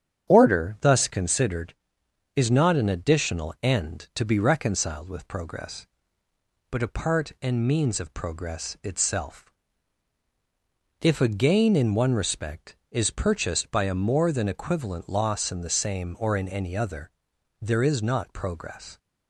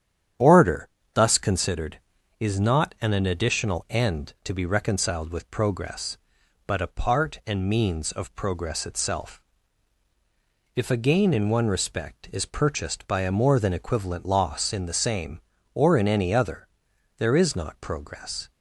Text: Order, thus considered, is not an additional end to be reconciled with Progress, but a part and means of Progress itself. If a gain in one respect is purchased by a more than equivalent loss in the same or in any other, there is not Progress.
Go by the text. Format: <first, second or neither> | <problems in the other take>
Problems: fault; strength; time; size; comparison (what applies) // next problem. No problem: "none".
first | starts louder than the rest; strong; until 1.6 s; 9.5 dB; strong in the first // says "an" twice; at 3.1 s